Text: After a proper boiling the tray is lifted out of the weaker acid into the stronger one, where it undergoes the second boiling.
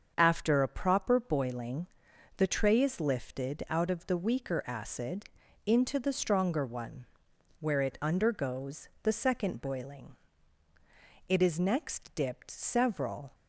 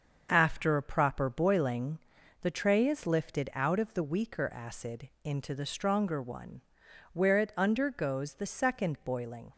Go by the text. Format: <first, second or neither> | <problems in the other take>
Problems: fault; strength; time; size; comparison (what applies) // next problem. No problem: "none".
second | starts louder than the rest; until 1.1 s; 7 dB; also in the second // pauses between "boiling" and "the"; noticeable; at 1.8 s; 0.48 s long; also in the second // pauses between "acid" and "into"; at 5.2 s; 0.42 s long // pauses between "undergoes" and "the"; slight; at 8.8 s; 0.16 s long // goes on to say "It is next dipped several"; strong; from 11.2 s on; 2.0 s long